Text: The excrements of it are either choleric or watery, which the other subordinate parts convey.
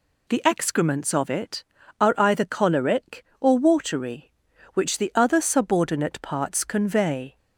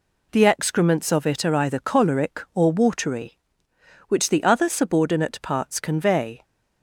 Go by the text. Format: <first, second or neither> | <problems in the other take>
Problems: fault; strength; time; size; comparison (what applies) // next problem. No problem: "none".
neither | none